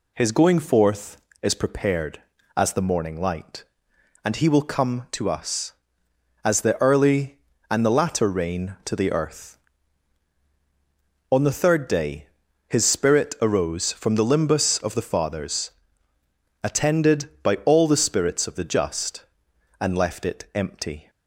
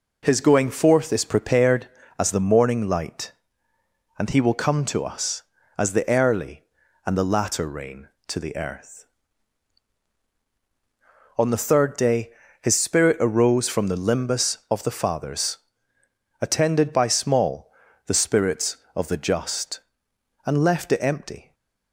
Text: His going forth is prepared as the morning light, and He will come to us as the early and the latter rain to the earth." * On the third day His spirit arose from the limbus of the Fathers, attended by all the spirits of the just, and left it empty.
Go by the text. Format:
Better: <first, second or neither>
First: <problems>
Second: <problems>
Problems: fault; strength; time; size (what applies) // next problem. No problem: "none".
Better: first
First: pauses between "day" and "His"; at 12.2 s; 0.40 s long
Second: pauses between "day" and "His"; slight; at 12.2 s; 0.32 s long // says "small" for "all"; at 17.0 s // stays silent after the last word; slight; from 21.4 s on; 0.5 s long